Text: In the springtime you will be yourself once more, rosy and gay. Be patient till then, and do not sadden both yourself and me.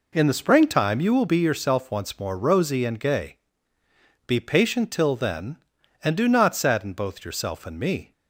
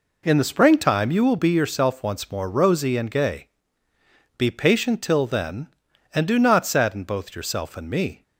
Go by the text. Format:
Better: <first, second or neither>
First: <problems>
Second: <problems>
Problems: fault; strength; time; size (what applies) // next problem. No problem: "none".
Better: neither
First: none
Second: none